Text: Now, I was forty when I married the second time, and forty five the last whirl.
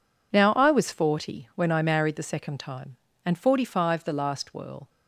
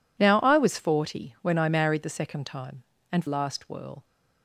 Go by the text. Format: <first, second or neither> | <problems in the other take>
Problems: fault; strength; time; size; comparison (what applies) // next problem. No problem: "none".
first | skips "forty five the"; at 3.2 s